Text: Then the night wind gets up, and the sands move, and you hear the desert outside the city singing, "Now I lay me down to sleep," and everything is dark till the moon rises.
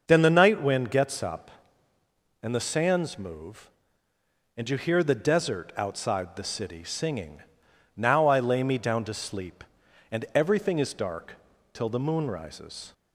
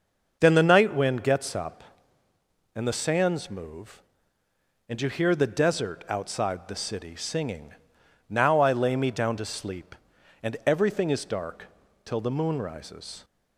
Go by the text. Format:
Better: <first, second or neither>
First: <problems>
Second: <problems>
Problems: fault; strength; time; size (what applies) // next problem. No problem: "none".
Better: neither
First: starts louder than the rest; until 1.0 s; 6 dB // pauses between "dark" and "till"; slight; at 11.3 s; 0.36 s long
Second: starts louder than the rest; until 1.4 s; 6 dB // pauses between "dark" and "till"; slight; at 11.6 s; 0.36 s long